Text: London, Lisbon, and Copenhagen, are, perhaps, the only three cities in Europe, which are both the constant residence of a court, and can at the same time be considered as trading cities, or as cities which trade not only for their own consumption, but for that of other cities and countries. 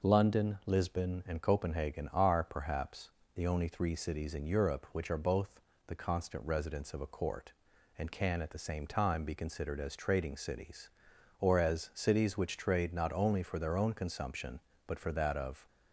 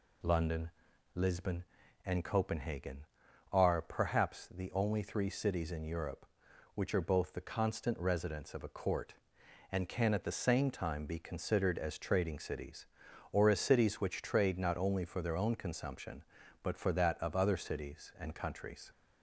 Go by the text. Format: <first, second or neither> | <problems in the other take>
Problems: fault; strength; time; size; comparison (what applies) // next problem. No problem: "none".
second | pauses between "both" and "the"; slight; at 5.5 s; 0.26 s long // stops before "other cities and countries"; at 15.6 s